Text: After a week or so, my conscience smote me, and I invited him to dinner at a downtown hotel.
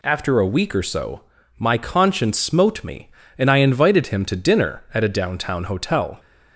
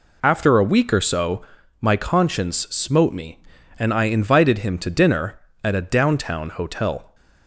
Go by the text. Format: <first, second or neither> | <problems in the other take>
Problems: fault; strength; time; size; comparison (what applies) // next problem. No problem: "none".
neither | none